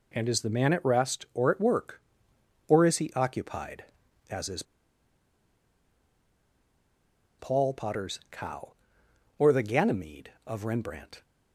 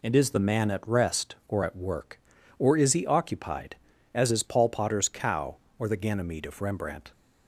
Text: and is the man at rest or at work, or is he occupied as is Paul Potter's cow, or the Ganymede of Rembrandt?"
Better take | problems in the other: second | pauses between "is" and "Paul"; strong; at 4.6 s; 2.7 s long

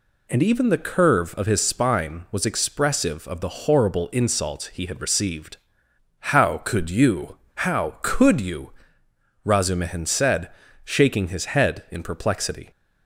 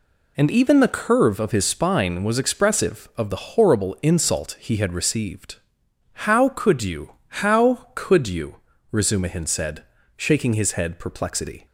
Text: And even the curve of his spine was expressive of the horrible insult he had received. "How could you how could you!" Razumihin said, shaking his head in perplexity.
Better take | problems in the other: first | pauses between "you" and "how"; slight; at 7.1 s; 0.20 s long; slight in the first // skips "in"; at 10.9 s

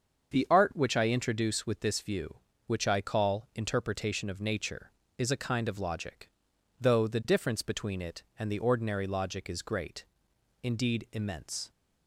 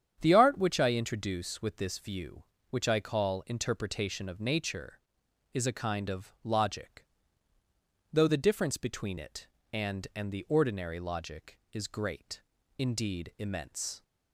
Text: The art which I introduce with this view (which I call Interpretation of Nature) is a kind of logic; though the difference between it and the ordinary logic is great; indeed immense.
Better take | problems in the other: first | starts louder than the rest; strong; until 1.2 s; 8.5 dB; also in the first // says "and" twice; at 10.1 s

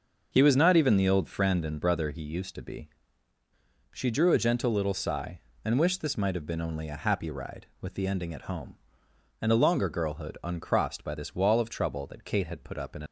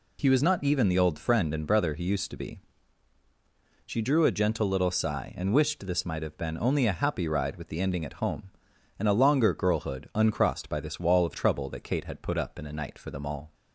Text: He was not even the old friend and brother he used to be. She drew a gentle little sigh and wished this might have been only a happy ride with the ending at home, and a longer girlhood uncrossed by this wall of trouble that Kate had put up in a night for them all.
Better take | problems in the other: second | starts louder than the rest; until 1.3 s; 6.5 dB // stops before "night for them all"; at 13.0 s

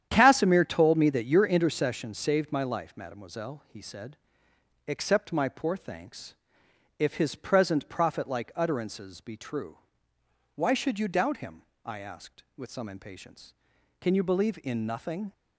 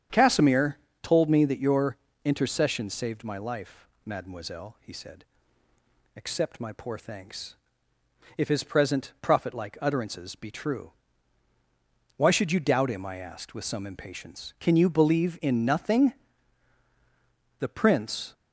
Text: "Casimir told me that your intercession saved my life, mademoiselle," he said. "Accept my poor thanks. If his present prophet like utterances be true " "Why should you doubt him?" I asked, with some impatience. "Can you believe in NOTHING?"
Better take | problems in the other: first | starts louder than the rest; strong; until 1.3 s; 8.5 dB; strong in the first // pauses between "Casimir" and "told"; slight; at 0.7 s; 0.26 s long // pauses between "your" and "intercession"; slight; at 1.9 s; 0.28 s long // goes on to say "The Prince"; noticeable; from 17.6 s on; 0.72 s long

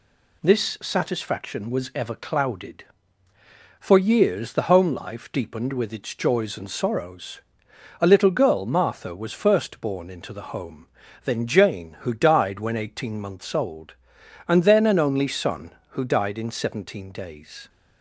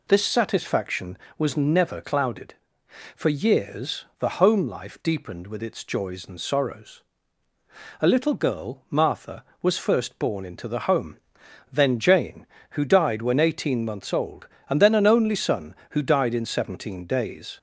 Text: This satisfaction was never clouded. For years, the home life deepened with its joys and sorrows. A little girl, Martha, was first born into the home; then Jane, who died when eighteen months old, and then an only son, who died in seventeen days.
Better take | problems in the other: second | says "ever" for "never"; at 1.9 s

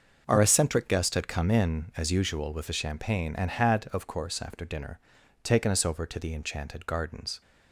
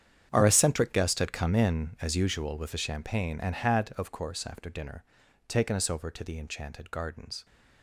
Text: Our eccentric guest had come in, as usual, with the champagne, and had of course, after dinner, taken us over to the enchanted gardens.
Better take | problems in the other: first | gets quieter; strong; throughout; 16 dB // starts louder than the rest; strong; until 1.3 s; 8.5 dB; noticeable in the first

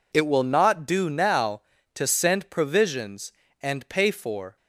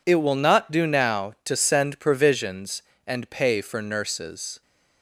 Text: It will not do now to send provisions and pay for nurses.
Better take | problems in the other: second | stops before "nurses"; at 4.5 s

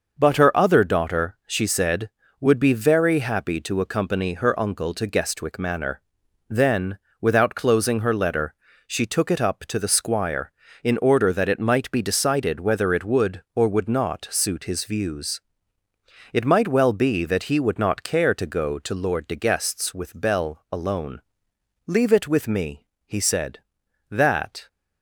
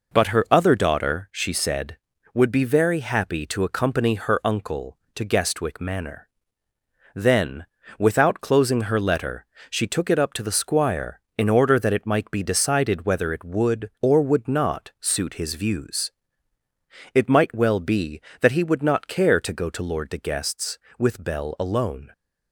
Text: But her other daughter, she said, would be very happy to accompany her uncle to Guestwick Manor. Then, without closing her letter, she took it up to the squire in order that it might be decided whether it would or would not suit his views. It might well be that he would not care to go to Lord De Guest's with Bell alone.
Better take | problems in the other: second | goes on to say "Leave it with me he said that"; strong; from 21.8 s on; 2.8 s long

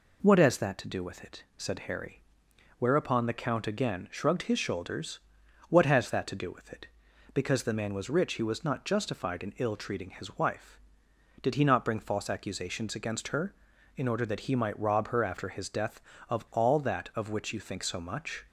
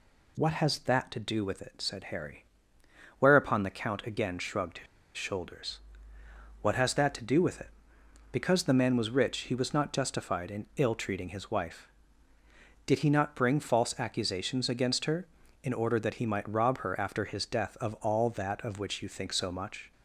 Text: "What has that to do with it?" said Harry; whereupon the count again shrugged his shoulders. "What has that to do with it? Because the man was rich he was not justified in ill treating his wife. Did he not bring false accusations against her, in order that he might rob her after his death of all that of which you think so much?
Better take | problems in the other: first | pauses between "his" and "shoulders"; slight; at 4.8 s; 0.31 s long

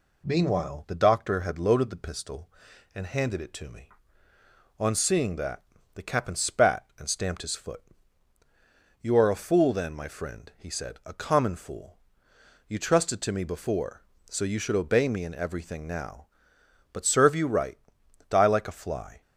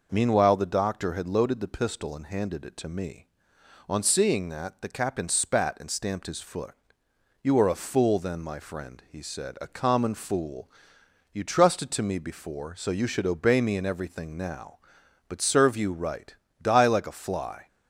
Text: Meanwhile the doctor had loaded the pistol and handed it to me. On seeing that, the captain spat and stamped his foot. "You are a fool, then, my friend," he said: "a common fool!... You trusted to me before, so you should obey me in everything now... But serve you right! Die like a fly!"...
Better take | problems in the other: neither | none

